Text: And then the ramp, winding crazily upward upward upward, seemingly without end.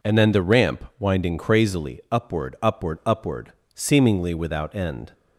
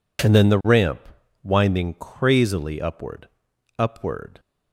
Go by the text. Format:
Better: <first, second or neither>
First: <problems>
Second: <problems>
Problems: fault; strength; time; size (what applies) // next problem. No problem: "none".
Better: first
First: none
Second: pauses between "upward" and "upward"; noticeable; at 3.2 s; 0.50 s long // stops before "upward seemingly without end"; at 4.3 s